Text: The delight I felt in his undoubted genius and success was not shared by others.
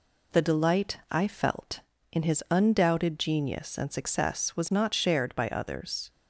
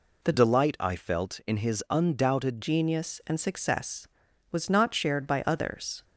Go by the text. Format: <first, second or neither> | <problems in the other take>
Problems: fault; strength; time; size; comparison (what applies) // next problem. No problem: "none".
first | changes voice from "delight" to "undoubted"; from 0.3 to 2.6 s; 2.3 s long